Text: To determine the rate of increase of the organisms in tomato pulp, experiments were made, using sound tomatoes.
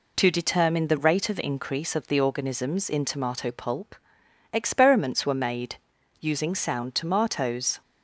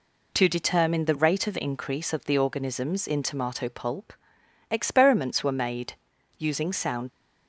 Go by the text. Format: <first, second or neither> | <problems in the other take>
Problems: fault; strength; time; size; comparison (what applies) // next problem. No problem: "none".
first | stops before "tomatoes"; at 7.1 s